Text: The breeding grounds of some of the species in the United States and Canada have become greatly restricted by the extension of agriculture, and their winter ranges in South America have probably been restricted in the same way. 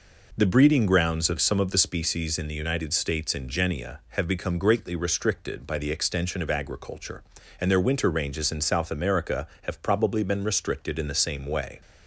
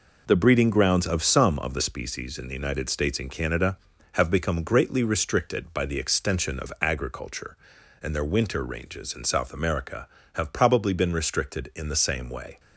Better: second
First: says "Genia" for "Canada"; at 3.4 s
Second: none

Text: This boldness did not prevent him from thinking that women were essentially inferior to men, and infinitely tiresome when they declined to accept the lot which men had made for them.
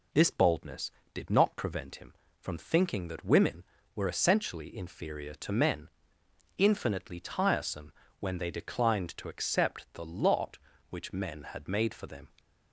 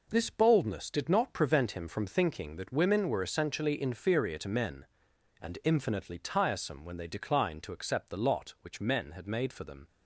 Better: second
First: skips "and"; at 6.2 s // pauses between "tiresome" and "when"; slight; at 7.9 s; 0.26 s long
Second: none

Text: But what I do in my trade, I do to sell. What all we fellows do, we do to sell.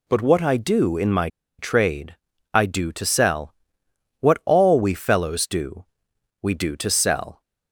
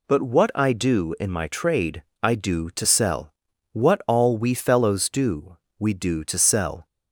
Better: second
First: pauses between "my" and "trade"; slight; at 1.2 s; 0.30 s long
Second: none

